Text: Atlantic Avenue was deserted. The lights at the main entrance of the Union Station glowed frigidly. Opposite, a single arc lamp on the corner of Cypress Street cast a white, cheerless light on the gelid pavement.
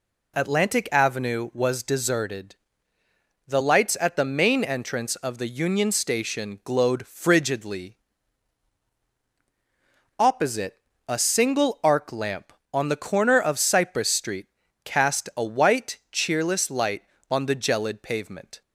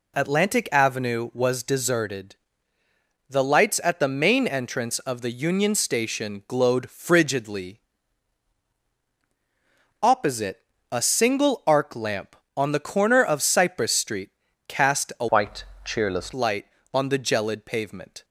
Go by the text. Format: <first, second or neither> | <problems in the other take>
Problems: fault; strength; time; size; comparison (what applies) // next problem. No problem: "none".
first | pauses between "Street" and "cast"; at 14.2 s; 0.40 s long; also in the first // changes voice from "white" to "cheerless"; from 15.2 to 16.3 s; 1.1 s long